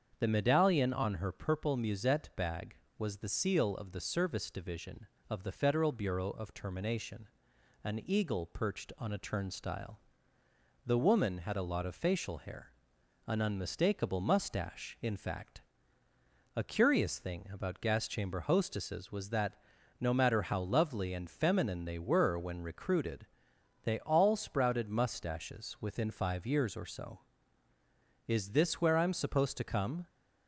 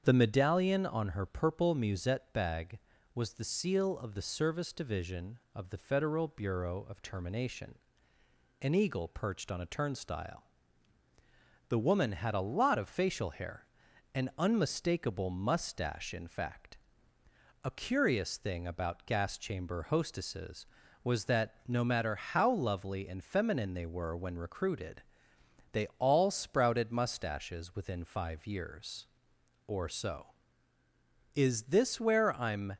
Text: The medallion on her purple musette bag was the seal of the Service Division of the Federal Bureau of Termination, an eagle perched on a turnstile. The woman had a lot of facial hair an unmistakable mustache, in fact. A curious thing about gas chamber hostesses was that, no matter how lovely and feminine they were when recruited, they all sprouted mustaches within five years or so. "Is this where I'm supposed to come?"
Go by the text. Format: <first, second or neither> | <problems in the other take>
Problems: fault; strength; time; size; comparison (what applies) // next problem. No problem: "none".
first | starts louder than the rest; strong; until 1.0 s; 7.5 dB; strong in the first // pauses between "hair" and "an"; noticeable; at 13.6 s; 0.52 s long; noticeable in the first // stops before "supposed to come"; at 32.7 s